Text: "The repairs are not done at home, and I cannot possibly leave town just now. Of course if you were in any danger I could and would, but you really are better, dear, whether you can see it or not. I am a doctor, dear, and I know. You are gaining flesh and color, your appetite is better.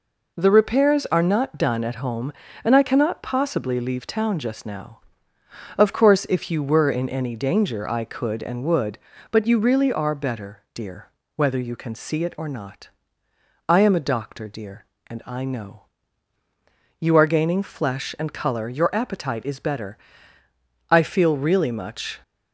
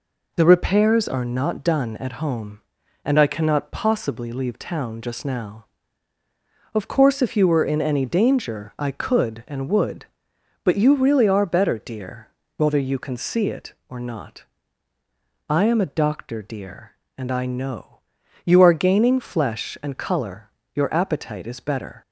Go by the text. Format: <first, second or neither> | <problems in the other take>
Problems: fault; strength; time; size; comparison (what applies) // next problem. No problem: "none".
second | goes on to say "I feel really much"; from 20.9 s on; 1.3 s long